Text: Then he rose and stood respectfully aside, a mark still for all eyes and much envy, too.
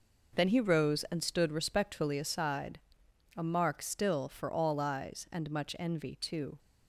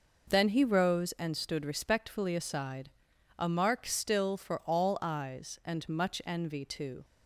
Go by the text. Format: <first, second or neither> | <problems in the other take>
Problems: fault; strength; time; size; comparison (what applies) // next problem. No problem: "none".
neither | none